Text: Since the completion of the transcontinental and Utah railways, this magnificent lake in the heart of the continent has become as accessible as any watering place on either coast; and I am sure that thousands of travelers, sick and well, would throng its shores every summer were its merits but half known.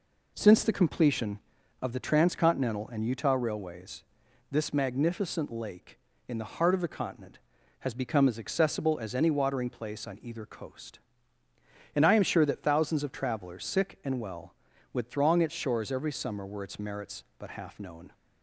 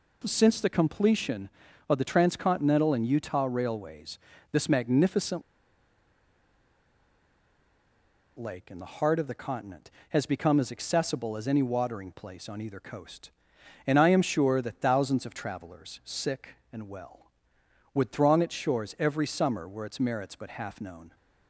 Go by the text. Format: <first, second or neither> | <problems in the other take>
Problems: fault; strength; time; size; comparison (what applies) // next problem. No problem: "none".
first | pauses between "magnificent" and "lake"; strong; at 5.4 s; 2.9 s long